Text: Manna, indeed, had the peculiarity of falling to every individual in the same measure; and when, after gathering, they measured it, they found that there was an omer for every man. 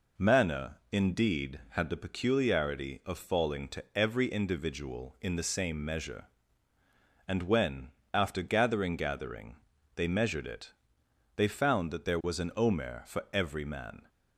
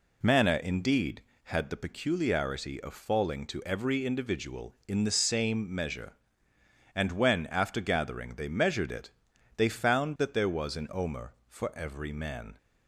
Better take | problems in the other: second | says "gathering" twice; at 8.9 s

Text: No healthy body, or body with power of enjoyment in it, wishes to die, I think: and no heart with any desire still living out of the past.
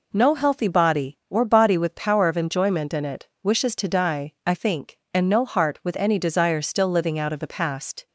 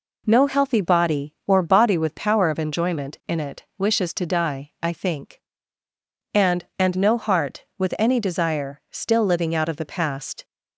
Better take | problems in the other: first | says "and" twice; at 6.7 s

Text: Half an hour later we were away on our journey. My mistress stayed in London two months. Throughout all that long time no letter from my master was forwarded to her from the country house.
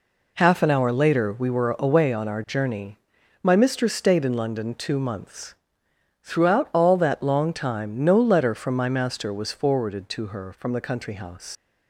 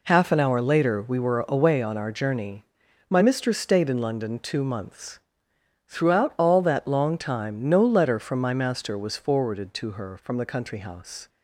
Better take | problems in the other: second | leaves "house" unfinished; at 11.5 s; 90 ms

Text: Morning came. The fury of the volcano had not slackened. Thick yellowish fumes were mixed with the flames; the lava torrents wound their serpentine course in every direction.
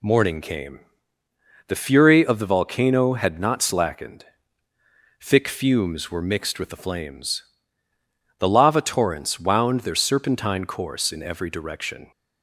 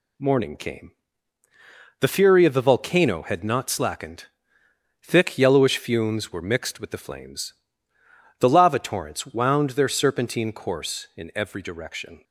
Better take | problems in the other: second | skips "yellowish"; at 5.4 s

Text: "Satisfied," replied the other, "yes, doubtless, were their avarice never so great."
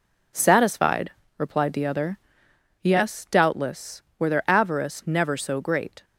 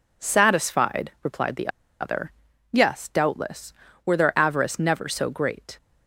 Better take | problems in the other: first | pauses between "the" and "other"; slight; at 1.6 s; 0.31 s long

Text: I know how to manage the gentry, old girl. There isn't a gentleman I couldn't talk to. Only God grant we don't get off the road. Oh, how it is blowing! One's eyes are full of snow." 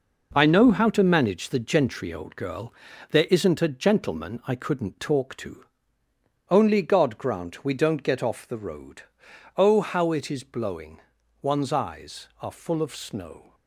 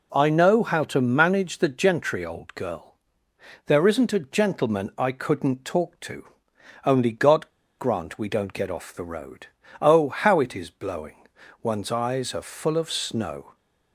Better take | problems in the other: first | pauses between "God" and "grant"; slight; at 7.4 s; 0.30 s long

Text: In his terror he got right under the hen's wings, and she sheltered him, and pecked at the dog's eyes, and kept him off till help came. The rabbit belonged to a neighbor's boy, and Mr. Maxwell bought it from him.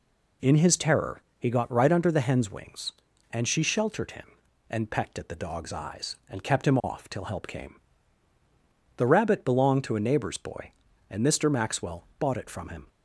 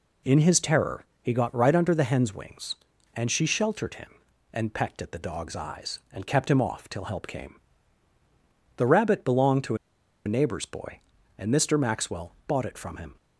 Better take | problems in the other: first | pauses between "terror" and "he"; slight; at 1.0 s; 0.16 s long; slight in the first // pauses between "to" and "a"; noticeable; at 9.7 s; 0.50 s long

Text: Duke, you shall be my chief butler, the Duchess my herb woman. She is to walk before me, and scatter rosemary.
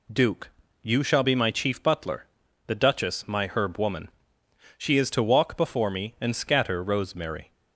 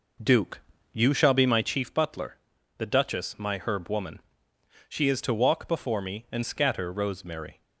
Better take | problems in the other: first | starts louder than the rest; noticeable; until 1.8 s; 5 dB

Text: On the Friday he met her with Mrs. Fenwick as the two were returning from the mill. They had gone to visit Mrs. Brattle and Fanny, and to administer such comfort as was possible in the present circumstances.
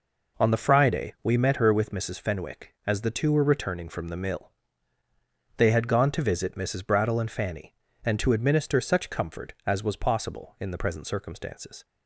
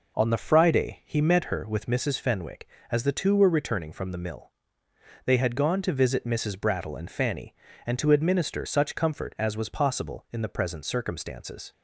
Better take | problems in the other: second | says "we" for "he"; at 1.2 s

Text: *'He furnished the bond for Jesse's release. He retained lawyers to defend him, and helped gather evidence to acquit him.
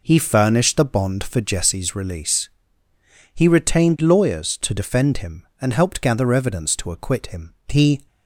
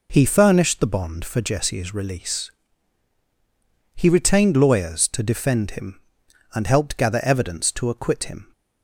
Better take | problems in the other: second | goes on to say "He"; slight; from 7.6 s on; 0.38 s long

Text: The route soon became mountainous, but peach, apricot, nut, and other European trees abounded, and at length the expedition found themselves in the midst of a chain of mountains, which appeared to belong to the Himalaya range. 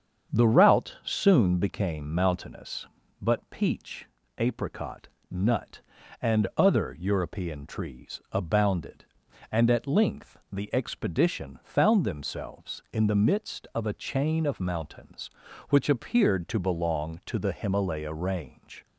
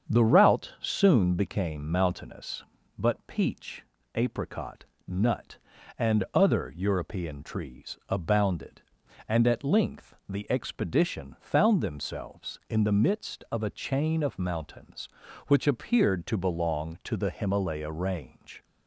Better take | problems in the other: neither | starts louder than the rest; strong; the same in both // pauses between "length" and "the"; slight; the same in both

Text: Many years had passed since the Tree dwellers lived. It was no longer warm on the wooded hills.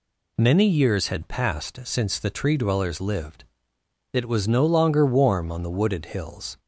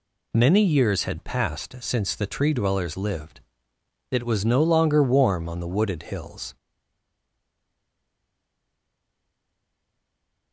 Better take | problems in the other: first | stays silent after the last word; strong; from 6.5 s on; 4.0 s long

